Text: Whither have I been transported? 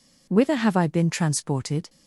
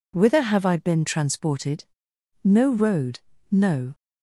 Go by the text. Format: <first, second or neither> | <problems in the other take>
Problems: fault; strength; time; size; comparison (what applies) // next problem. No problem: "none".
first | goes on to say "No road no"; from 2.4 s on; 1.5 s long